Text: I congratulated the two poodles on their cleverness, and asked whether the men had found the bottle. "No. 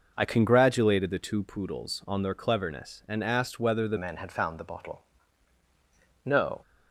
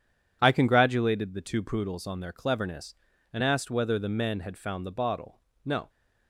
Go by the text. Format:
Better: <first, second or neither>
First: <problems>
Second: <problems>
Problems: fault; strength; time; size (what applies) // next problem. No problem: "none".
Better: second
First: changes voice at "men"; from 3.9 s on; 2.7 s long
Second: none